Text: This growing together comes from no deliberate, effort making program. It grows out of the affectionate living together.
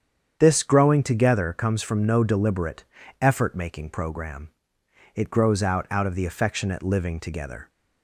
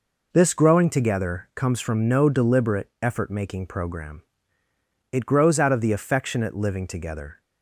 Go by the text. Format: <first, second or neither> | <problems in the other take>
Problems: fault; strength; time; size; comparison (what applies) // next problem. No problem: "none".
second | starts louder than the rest; strong; until 1.4 s; 8 dB // says "out" twice; at 5.9 s